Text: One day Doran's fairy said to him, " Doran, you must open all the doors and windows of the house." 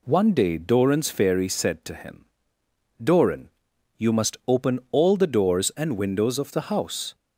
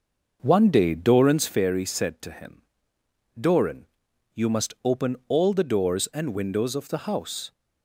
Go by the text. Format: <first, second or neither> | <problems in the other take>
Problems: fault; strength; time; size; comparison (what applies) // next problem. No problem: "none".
first | starts louder than the rest; until 1.6 s; 6 dB